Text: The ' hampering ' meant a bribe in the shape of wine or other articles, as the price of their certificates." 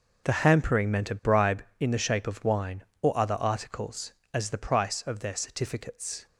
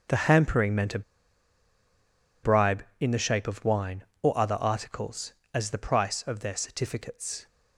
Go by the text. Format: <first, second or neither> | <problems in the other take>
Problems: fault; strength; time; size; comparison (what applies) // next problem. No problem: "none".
first | starts louder than the rest; strong; until 2.6 s; 7.5 dB; strong in the first // pauses between "a" and "bribe"; strong; at 1.0 s; 1.4 s long